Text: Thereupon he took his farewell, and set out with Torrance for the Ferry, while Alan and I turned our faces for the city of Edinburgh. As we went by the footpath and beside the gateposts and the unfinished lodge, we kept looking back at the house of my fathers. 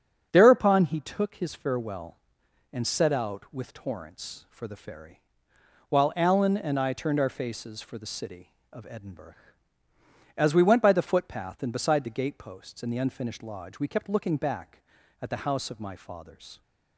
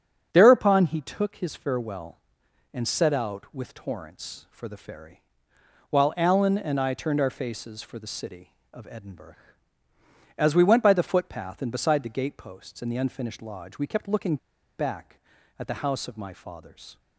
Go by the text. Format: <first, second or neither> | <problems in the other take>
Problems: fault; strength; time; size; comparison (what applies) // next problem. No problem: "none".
first | starts louder than the rest; until 1.3 s; 7 dB; also in the first // pauses between "looking" and "back"; at 14.3 s; 0.41 s long